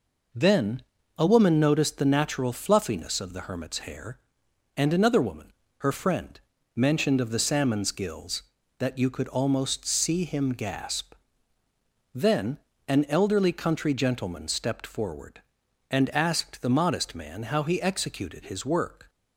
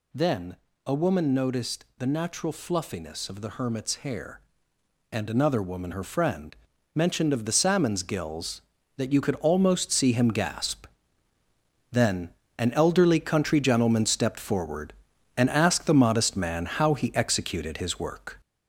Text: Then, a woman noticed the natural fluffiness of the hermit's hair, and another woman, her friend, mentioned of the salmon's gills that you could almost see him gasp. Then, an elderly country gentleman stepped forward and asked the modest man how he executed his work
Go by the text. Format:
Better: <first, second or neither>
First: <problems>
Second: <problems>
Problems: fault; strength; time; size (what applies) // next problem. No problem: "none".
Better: first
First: none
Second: gets louder; noticeable; throughout; 4 dB